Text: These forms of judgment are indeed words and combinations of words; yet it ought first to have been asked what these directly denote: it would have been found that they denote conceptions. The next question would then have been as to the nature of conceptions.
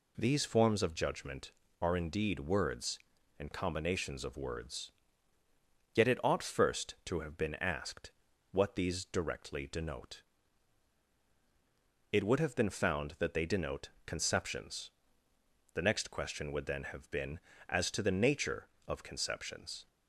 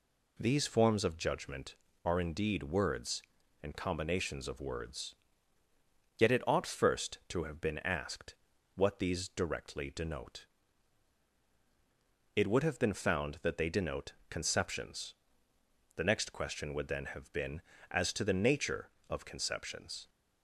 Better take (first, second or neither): neither